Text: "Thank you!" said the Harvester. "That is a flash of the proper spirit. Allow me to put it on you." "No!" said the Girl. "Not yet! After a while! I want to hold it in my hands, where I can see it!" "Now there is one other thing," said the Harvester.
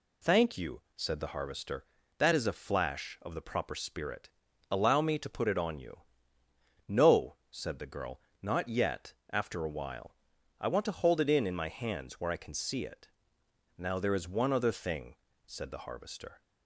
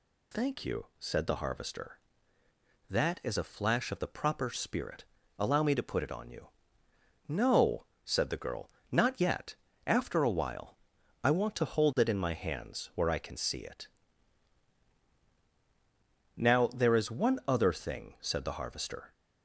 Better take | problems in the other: second | says "in" twice; at 11.4 s

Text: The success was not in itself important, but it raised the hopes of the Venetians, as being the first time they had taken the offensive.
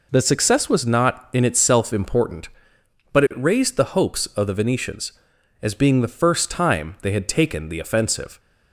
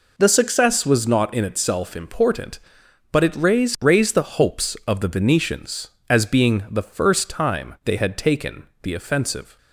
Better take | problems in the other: first | says "raised" twice; at 3.8 s

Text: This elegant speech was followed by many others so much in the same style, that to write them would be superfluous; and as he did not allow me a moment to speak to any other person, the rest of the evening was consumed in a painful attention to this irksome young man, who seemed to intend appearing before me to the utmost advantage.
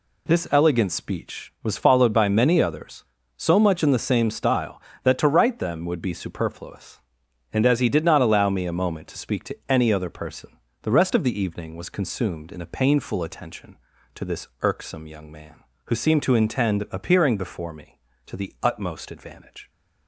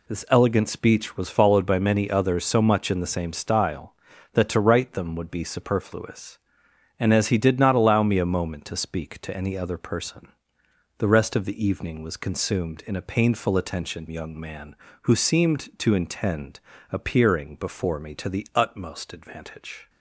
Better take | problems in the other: first | skips "to this irksome"; at 14.0 s // pauses between "intend" and "appearing"; slight; at 16.6 s; 0.28 s long

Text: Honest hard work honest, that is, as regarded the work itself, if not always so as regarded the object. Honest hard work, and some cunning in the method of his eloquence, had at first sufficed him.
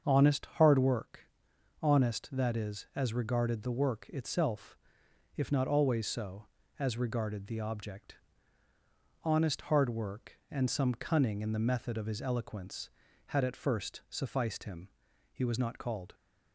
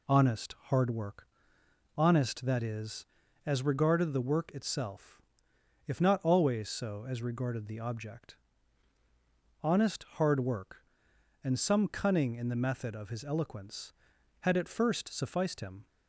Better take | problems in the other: second | starts louder than the rest; until 1.1 s; 7 dB // pauses between "work" and "honest"; noticeable; at 1.1 s; 0.62 s long; noticeable in the second // goes on to say "He was not called"; noticeable; from 15.3 s on; 0.82 s long

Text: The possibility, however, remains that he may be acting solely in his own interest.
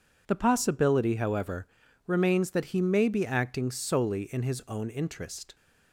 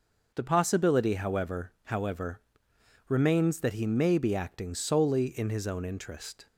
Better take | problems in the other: first | says "however" twice; at 1.8 s

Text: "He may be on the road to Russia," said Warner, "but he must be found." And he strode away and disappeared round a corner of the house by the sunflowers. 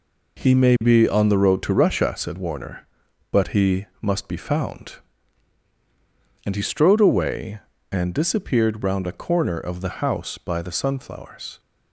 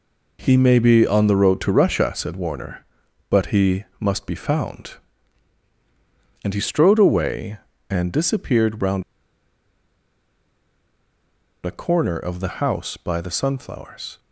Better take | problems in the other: first | pauses between "he" and "must"; slight; at 3.8 s; 0.16 s long; slight in the first // pauses between "round" and "a"; strong; at 9.0 s; 2.6 s long

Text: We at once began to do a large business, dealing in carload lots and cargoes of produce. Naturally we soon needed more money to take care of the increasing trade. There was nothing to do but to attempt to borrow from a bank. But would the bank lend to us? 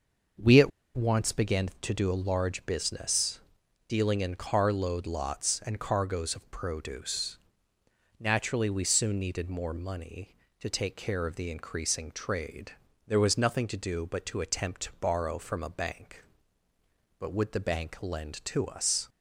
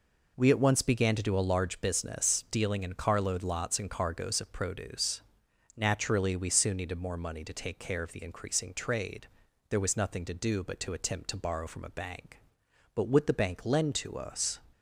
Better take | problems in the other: second | starts louder than the rest; noticeable; until 1.6 s; 6 dB // pauses between "at" and "once"; slight; at 0.7 s; 0.26 s long

